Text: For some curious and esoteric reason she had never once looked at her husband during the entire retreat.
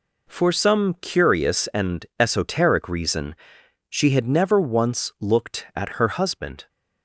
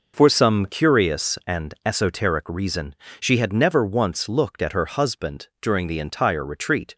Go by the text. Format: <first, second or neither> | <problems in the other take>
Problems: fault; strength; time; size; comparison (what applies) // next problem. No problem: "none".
second | pauses between "and" and "esoteric"; slight; at 2.0 s; 0.16 s long // pauses between "reason" and "she"; noticeable; at 3.3 s; 0.54 s long; slight in the second // stops before "during the entire retreat"; at 6.6 s